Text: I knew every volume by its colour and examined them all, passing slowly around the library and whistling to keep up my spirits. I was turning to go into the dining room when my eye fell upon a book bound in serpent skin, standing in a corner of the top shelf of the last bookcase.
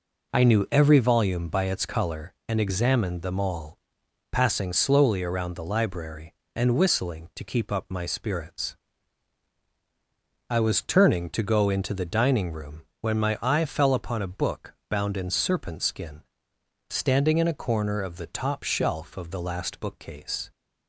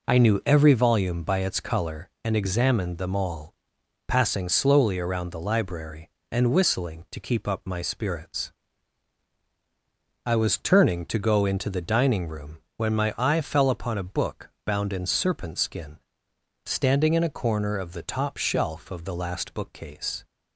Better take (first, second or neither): neither